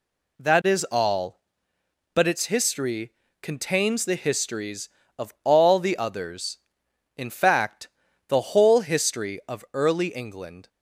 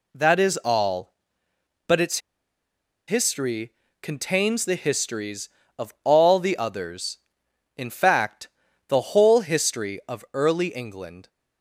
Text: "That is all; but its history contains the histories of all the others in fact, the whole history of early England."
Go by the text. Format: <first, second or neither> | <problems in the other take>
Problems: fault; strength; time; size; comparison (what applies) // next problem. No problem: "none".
first | pauses between "its" and "history"; noticeable; at 2.1 s; 0.88 s long // pauses between "history" and "contains"; slight; at 3.7 s; 0.26 s long; slight in the first